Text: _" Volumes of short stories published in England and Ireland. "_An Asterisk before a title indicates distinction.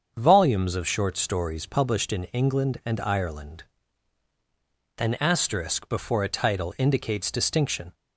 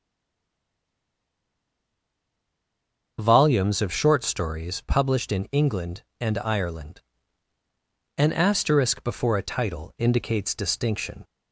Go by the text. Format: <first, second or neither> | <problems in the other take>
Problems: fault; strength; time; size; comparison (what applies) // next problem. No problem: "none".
first | stays silent before the first word; strong; until 3.1 s; 3.1 s long // starts louder than the rest; until 4.1 s; 6.5 dB; also in the first